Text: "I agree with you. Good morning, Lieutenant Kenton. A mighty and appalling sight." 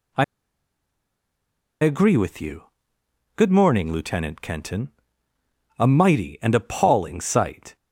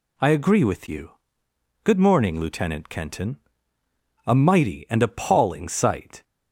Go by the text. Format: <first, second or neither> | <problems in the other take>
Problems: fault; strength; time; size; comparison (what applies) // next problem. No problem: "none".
second | pauses between "I" and "agree"; strong; at 0.2 s; 1.5 s long